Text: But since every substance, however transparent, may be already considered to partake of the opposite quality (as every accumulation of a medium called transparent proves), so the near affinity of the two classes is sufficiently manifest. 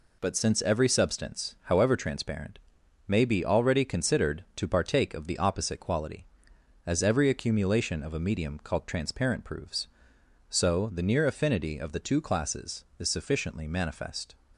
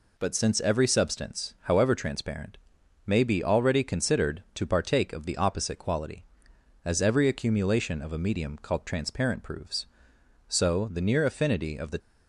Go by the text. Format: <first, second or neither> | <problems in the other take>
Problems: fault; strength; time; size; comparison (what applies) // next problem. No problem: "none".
first | stops before "two classes is sufficiently manifest"; at 11.9 s